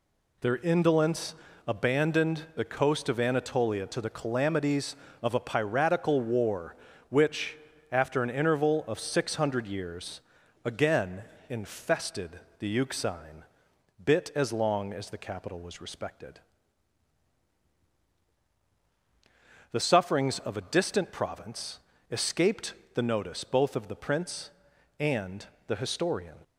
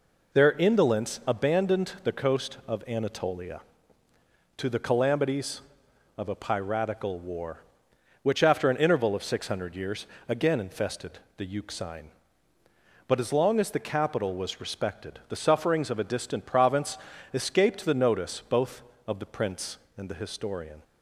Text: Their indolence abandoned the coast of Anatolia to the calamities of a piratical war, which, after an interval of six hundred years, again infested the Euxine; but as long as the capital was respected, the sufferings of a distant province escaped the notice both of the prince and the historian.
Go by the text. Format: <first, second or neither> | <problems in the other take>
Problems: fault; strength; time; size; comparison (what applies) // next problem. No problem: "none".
second | pauses between "indolence" and "abandoned"; slight; at 1.3 s; 0.32 s long // pauses between "again" and "infested"; slight; at 11.2 s; 0.26 s long // pauses between "infested" and "the"; slight; at 12.3 s; 0.20 s long; slight in the second // says "bit" for "but"; at 14.0 s // pauses between "province" and "escaped"; slight; at 21.7 s; 0.30 s long; slight in the second // pauses between "escaped" and "the"; slight; at 22.7 s; 0.20 s long // pauses between "and" and "the"; slight; at 25.4 s; 0.20 s long